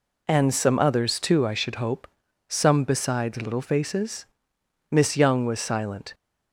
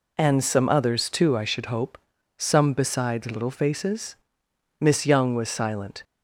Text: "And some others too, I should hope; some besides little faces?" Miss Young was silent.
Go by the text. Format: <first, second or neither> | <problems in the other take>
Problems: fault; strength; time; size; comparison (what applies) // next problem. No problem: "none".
neither | none